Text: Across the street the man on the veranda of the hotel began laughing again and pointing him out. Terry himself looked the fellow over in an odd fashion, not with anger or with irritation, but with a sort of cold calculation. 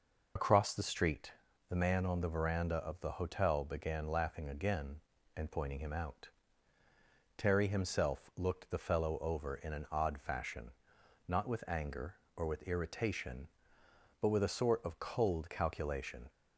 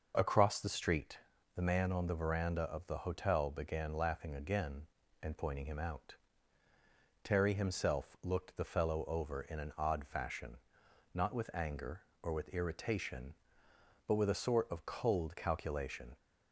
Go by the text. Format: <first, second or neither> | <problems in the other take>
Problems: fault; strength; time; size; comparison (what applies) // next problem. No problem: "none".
second | loses the start of "Across"; at 0.3 s; 70 ms // pauses between "street" and "the"; at 1.3 s; 0.38 s long; also in the second